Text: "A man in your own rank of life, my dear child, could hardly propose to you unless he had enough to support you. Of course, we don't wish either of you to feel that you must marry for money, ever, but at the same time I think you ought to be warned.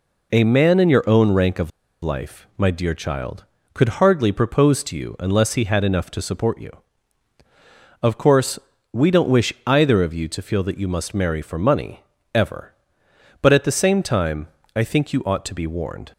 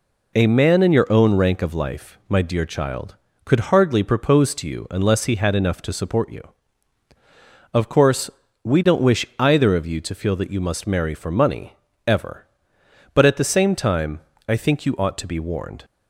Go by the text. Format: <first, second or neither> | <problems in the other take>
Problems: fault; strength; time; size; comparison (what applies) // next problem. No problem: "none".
second | pauses between "of" and "life"; slight; at 1.7 s; 0.33 s long // pauses between "time" and "I"; slight; at 14.4 s; 0.30 s long; slight in the second